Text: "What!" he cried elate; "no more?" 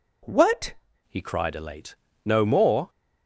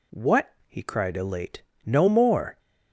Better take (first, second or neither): second